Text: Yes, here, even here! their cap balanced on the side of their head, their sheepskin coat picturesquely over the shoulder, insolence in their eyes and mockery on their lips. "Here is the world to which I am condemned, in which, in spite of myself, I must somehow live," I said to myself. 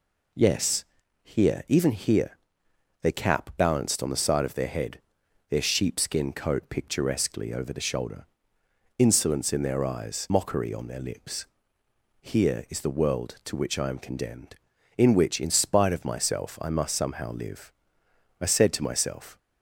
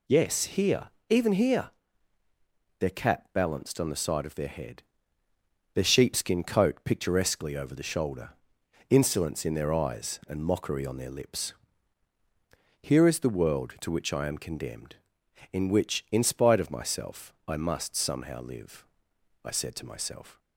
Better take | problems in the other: second | skips "and"; at 10.2 s

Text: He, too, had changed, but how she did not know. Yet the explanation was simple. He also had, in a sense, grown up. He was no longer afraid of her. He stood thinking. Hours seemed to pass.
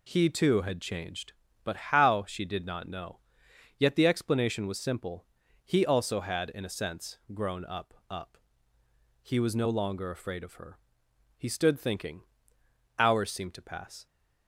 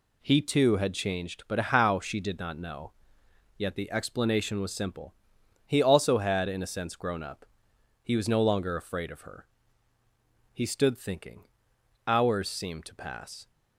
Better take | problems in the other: second | says "up" twice; at 8.0 s

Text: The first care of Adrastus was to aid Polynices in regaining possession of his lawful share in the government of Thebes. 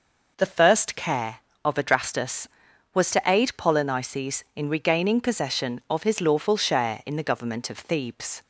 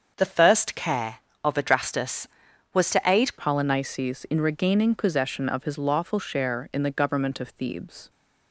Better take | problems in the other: first | starts louder than the rest; until 1.1 s; 7 dB // changes voice at "Polynices"; from 3.3 s on; 4.7 s long

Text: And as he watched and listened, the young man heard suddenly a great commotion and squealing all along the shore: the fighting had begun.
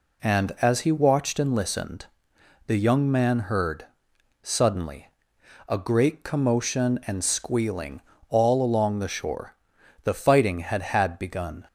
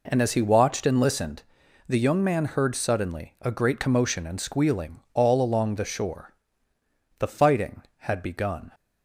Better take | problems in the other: second | pauses between "heard" and "suddenly"; noticeable; at 3.8 s; 0.56 s long // pauses between "suddenly" and "a"; noticeable; at 5.0 s; 0.60 s long // pauses between "squealing" and "all"; slight; at 8.0 s; 0.26 s long // says "had" twice; at 10.8 s

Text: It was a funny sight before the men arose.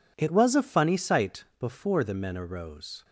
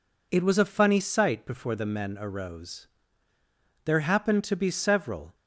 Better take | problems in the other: first | goes on to say "There happened to be several"; from 3.8 s on; 1.5 s long

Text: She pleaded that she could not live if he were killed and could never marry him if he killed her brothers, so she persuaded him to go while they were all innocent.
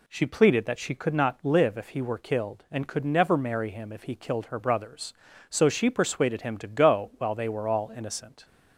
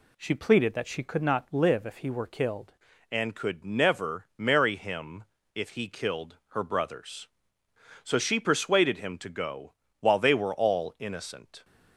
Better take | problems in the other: first | changes voice at "and"; from 3.1 s on; 8.5 s long // pauses between "him" and "if"; slight; at 5.2 s; 0.30 s long // pauses between "go" and "while"; slight; at 9.7 s; 0.28 s long

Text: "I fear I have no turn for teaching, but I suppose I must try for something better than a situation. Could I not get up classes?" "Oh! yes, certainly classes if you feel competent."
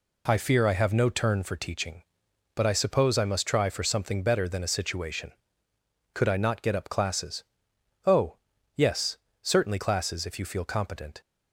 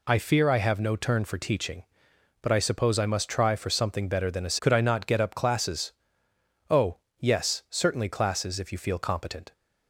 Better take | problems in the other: first | skips "situation"; at 4.5 s

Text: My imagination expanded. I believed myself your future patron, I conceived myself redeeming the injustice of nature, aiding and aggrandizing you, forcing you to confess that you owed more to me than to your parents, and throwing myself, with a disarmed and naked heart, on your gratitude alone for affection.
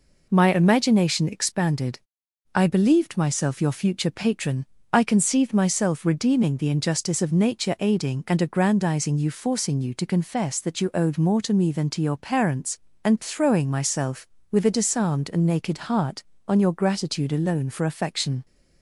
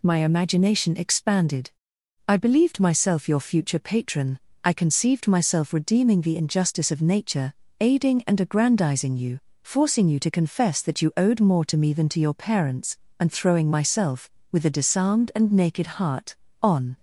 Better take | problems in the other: first | stops before "your gratitude alone for affection"; at 16.9 s

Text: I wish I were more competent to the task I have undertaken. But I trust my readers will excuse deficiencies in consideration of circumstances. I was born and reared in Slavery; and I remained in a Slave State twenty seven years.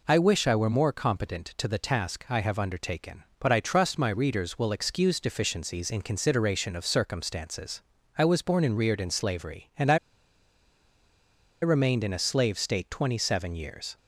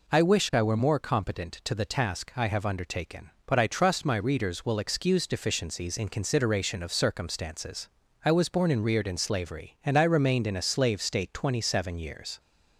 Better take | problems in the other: second | pauses between "I" and "remained"; strong; at 9.9 s; 1.6 s long

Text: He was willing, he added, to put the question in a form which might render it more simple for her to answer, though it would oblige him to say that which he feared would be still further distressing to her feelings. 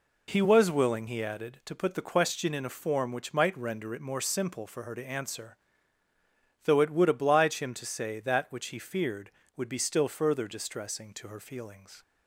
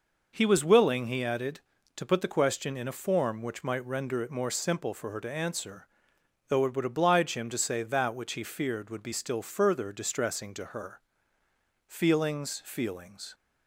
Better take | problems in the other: first | pauses between "her" and "feelings"; noticeable; at 11.0 s; 0.86 s long // says "feelings" twice; at 12.6 s

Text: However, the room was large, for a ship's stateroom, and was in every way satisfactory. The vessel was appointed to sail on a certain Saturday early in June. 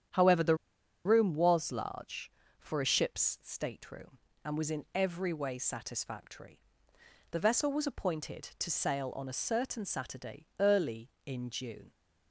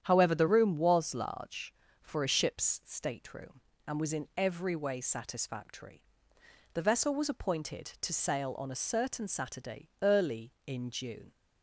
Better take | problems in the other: second | starts louder than the rest; strong; until 1.6 s; 9 dB; strong in the second // pauses between "the" and "room"; noticeable; at 0.5 s; 0.48 s long

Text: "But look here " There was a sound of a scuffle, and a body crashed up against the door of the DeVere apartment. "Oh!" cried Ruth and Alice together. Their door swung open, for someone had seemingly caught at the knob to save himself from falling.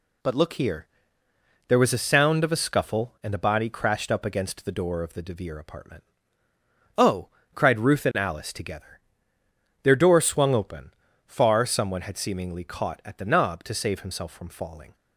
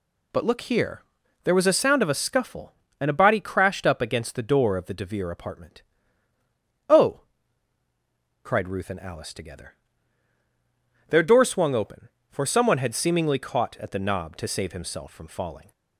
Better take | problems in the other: second | says "far" for "for"; at 11.2 s

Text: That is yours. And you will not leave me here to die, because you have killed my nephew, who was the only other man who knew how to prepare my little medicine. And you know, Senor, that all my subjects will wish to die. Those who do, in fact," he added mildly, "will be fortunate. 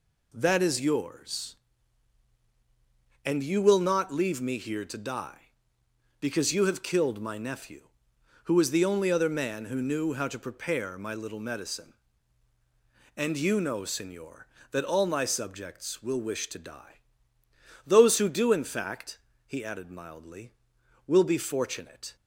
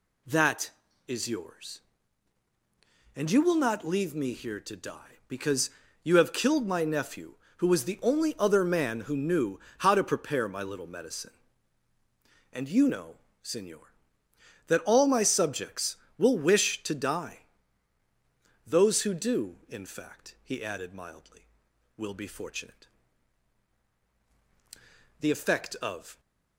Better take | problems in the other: first | pauses between "because" and "you"; slight; at 5.6 s; 0.34 s long // pauses between "knew" and "how"; slight; at 9.5 s; 0.20 s long // goes on to say "The effect of"; noticeable; from 25.2 s on; 0.98 s long

